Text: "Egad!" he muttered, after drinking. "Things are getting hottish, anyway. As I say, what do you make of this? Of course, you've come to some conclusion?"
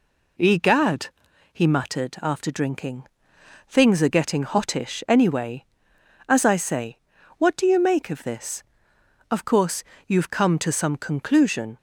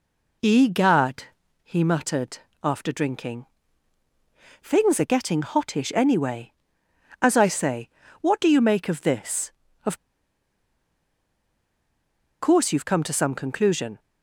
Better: first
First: none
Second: pauses between "Of" and "course"; strong; at 9.9 s; 2.4 s long

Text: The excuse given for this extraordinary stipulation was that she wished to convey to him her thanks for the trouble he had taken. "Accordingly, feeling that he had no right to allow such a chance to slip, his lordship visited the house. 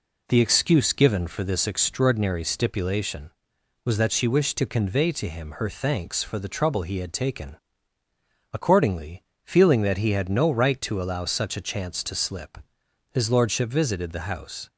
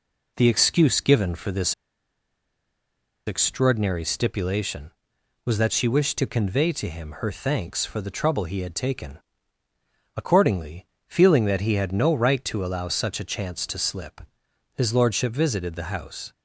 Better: first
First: none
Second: pauses between "this" and "extraordinary"; strong; at 1.7 s; 1.5 s long

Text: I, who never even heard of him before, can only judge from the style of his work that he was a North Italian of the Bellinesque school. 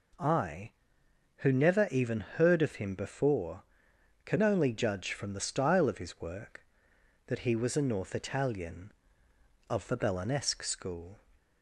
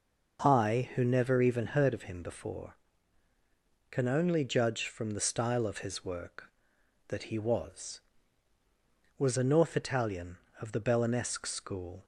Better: first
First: none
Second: says "was" twice; at 9.1 s

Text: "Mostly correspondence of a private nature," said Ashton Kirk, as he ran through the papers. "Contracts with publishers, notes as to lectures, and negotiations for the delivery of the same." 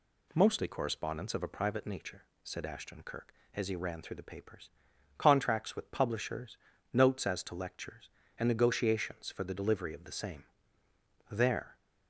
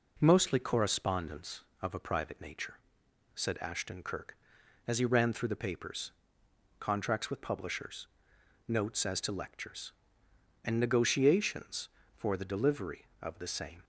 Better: second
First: goes on to say "There"; slight; from 11.3 s on; 0.46 s long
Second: none

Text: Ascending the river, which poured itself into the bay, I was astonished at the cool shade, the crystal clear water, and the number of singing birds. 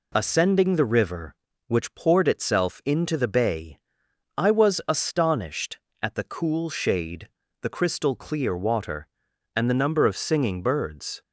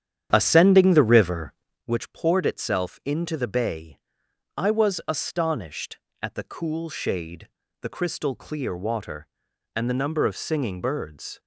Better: first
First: none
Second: starts louder than the rest; strong; until 1.9 s; 9.5 dB

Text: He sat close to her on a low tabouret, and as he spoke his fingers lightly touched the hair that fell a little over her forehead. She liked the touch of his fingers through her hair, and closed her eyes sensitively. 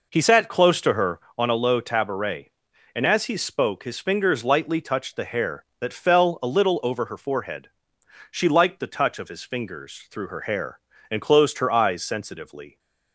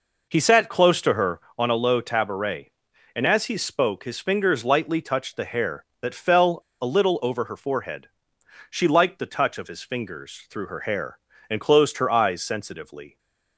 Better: first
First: none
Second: pauses between "fell" and "a"; slight; at 6.5 s; 0.21 s long

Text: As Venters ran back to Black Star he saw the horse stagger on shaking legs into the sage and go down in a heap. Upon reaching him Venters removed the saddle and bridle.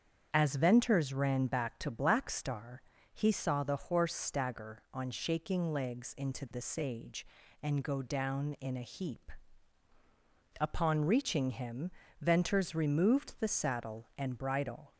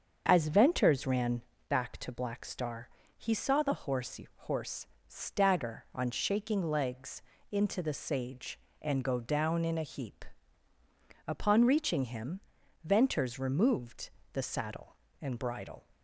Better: first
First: starts louder than the rest; strong; until 1.3 s; 7.5 dB // pauses between "Star" and "he"; slight; at 2.8 s; 0.30 s long // pauses between "him" and "Venters"; slight; at 11.9 s; 0.28 s long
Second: starts louder than the rest; until 1.2 s; 6.5 dB // pauses between "ran" and "back"; slight; at 1.4 s; 0.28 s long // pauses between "Star" and "he"; slight; at 2.8 s; 0.28 s long // says "horse" twice; at 4.4 s // pauses between "legs" and "into"; slight; at 7.2 s; 0.28 s long // pauses between "him" and "Venters"; at 12.4 s; 0.44 s long // pauses between "removed" and "the"; slight; at 14.1 s; 0.24 s long

